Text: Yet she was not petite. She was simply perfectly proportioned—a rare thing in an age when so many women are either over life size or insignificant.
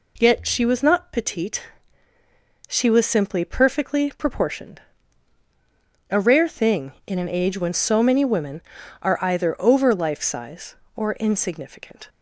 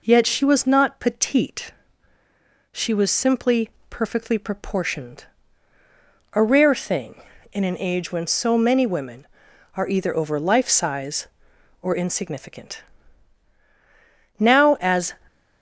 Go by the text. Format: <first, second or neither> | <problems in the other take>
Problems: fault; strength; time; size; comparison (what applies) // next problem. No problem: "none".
first | pauses between "simply" and "perfectly"; slight; at 3.6 s; 0.18 s long // goes on to say "Now as"; noticeable; from 14.3 s on; 0.76 s long